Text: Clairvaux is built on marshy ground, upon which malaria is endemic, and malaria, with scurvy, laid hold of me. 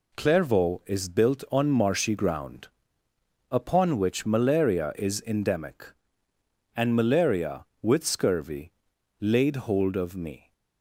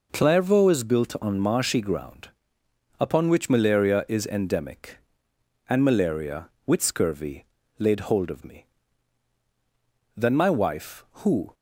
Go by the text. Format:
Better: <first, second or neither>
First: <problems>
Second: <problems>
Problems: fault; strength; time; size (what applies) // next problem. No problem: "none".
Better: first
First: none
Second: goes on to say "Then my wife who"; from 10.1 s on; 1.3 s long